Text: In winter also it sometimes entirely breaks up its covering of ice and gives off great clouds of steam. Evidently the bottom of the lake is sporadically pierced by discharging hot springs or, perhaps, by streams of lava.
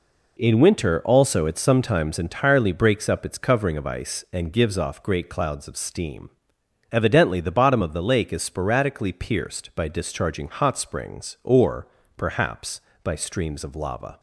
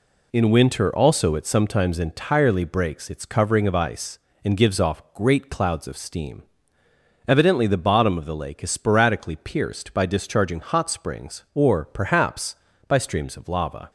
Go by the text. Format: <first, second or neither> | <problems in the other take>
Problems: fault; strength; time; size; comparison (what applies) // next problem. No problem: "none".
first | skips "up"; at 3.1 s